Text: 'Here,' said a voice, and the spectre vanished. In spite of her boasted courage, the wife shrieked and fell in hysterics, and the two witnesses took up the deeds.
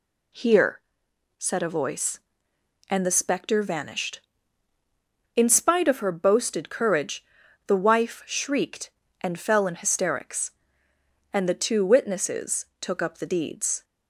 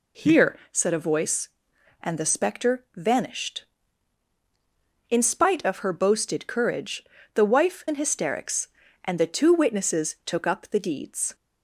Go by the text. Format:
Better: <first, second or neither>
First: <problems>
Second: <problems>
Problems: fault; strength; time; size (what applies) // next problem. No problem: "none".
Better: first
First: none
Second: skips "shrieked and fell"; at 7.8 s